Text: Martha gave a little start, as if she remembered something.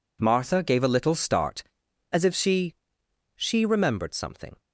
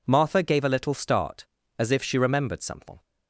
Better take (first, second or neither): second